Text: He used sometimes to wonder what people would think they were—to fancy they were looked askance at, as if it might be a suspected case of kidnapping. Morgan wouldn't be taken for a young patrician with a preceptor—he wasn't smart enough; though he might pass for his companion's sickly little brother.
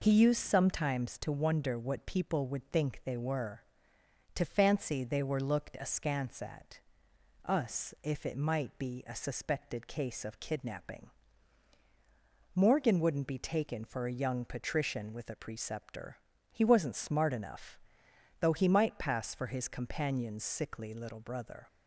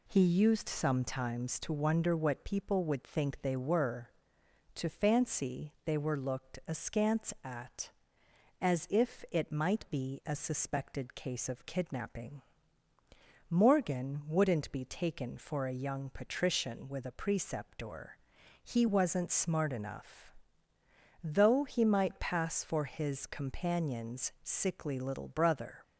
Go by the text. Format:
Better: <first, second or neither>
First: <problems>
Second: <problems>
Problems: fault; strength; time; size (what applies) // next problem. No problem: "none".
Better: second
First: says "us" for "as"; at 7.4 s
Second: none